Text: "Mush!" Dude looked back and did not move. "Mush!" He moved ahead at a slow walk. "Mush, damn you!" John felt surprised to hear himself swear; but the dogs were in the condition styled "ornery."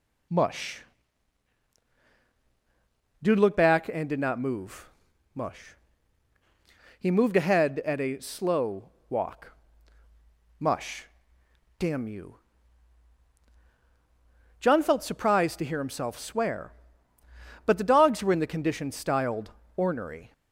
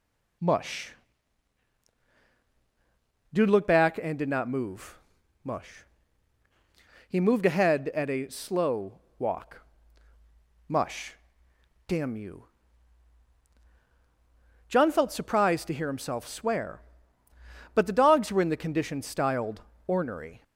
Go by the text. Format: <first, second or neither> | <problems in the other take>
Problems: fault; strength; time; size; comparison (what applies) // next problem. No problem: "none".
neither | pauses between "slow" and "walk"; slight; the same in both // pauses between "styled" and "ornery"; slight; the same in both